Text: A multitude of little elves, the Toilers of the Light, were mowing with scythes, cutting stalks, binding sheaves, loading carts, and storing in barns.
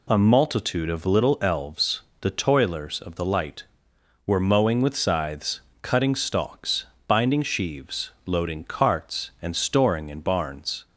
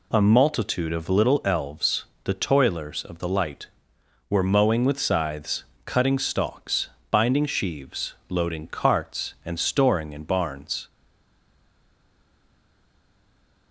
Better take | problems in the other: first | stays silent after the last word; strong; from 10.8 s on; 2.9 s long

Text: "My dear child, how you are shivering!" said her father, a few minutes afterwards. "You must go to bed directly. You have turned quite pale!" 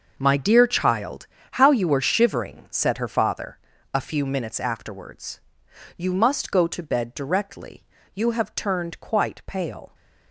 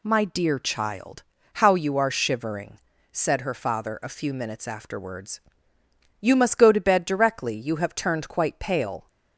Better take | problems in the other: second | gets quieter; strong; throughout; 12 dB

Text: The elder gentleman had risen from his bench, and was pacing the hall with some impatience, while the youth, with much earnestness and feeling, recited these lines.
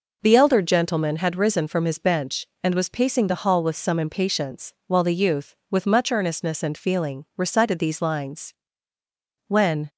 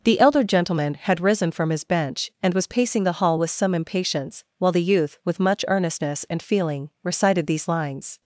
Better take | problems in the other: second | goes on to say "When"; slight; from 9.4 s on; 0.46 s long

